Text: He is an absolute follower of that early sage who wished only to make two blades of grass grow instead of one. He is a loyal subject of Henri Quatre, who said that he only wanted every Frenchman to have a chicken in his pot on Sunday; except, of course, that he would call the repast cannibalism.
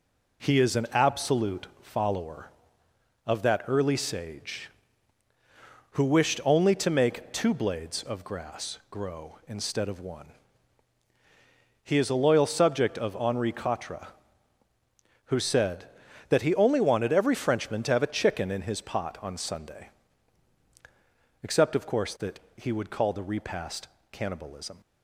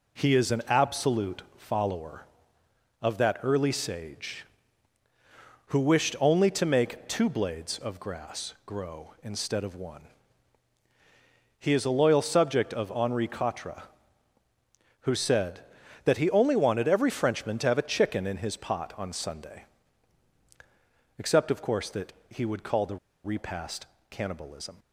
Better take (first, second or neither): first